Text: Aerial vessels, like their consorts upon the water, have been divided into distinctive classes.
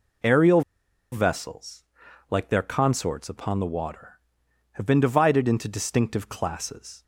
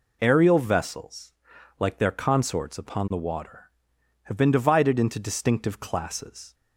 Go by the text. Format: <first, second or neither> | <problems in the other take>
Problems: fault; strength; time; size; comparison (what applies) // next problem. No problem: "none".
second | pauses between "Aerial" and "vessels"; noticeable; at 0.6 s; 0.51 s long